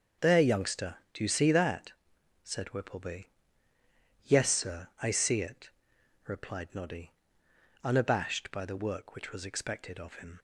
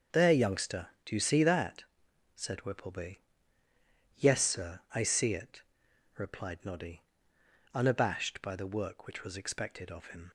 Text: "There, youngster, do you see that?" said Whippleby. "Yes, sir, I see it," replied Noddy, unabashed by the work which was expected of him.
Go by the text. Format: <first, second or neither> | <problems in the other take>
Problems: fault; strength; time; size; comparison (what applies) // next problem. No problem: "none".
neither | starts louder than the rest; the same in both